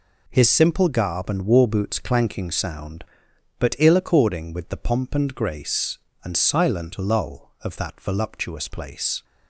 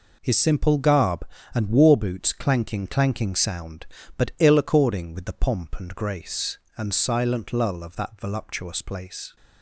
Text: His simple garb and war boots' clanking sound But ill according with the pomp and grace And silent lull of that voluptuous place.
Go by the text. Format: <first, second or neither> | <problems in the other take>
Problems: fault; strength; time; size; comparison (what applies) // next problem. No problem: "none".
first | says "clanking" twice; at 2.8 s